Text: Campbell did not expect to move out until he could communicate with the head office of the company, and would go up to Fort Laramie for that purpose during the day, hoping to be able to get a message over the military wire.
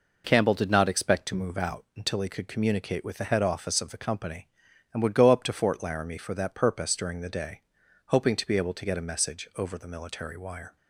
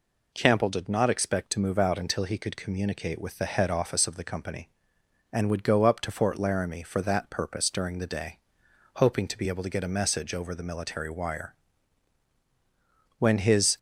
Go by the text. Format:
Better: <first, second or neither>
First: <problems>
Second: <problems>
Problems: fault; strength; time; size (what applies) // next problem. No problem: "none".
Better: first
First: none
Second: goes on to say "When his"; from 13.1 s on; 0.60 s long